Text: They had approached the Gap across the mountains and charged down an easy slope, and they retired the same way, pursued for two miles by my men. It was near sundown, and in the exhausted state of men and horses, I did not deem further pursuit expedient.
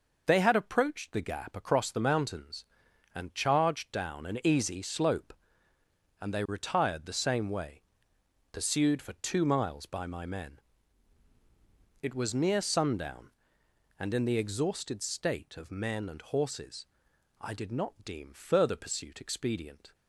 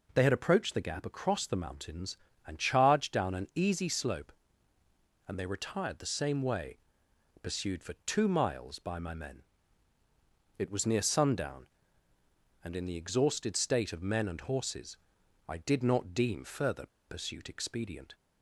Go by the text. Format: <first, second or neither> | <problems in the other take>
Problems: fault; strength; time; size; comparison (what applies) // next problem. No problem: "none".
first | pauses between "further" and "pursuit"; slight; at 16.8 s; 0.22 s long